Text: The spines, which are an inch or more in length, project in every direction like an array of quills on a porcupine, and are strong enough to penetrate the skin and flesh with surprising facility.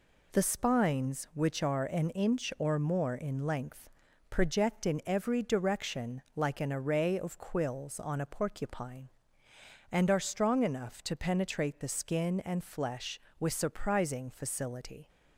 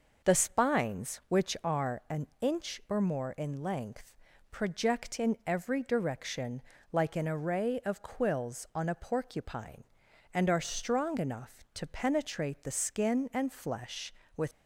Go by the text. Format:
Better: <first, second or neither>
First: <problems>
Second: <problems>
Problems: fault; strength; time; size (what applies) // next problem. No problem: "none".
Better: first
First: pauses between "direction" and "like"; slight; at 6.2 s; 0.16 s long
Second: pauses between "an" and "inch"; slight; at 2.2 s; 0.16 s long // pauses between "direction" and "like"; slight; at 6.6 s; 0.32 s long // stops before "surprising facility"; at 14.5 s